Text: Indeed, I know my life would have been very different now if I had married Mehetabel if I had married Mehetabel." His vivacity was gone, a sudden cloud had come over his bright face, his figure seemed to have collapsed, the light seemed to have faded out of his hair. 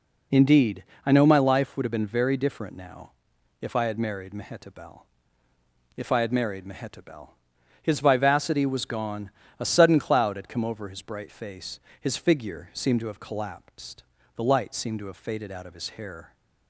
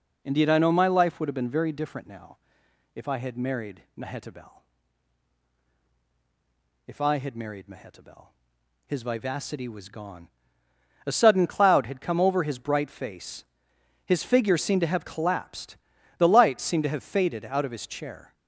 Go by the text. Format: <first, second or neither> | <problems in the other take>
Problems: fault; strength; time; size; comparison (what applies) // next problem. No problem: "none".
first | pauses between "now" and "if"; noticeable; at 2.3 s; 0.58 s long; noticeable in the first // pauses between "Mehetabel" and "if"; strong; at 4.5 s; 2.3 s long; noticeable in the first // says "chair" for "hair"; at 17.8 s